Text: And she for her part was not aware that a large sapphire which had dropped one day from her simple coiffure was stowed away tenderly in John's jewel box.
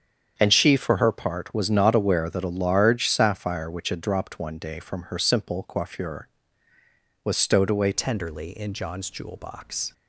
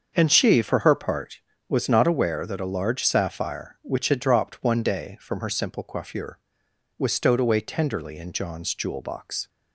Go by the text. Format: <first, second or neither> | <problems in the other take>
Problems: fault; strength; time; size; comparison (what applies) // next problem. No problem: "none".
second | starts louder than the rest; strong; until 1.3 s; 8 dB; also in the second // changes voice at "tenderly"; from 7.9 s on; 2.0 s long